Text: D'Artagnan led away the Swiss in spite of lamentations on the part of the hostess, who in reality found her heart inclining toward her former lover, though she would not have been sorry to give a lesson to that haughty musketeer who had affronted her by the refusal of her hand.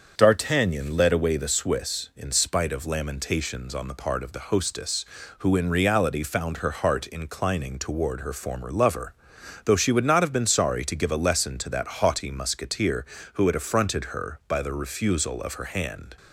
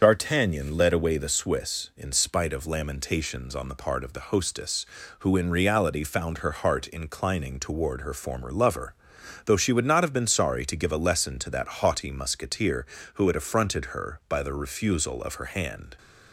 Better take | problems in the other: first | loses the start of "D'Artagnan"; at 0.0 s; 50 ms // starts louder than the rest; until 1.0 s; 7 dB; also in the first

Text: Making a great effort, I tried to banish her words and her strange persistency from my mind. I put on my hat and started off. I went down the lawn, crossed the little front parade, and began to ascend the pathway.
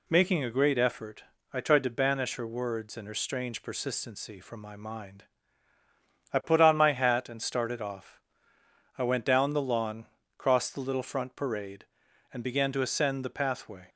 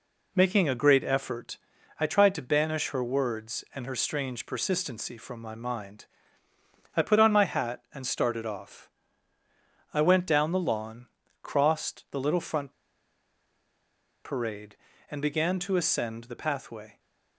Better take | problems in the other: first | pauses between "front" and "parade"; strong; at 12.7 s; 1.5 s long

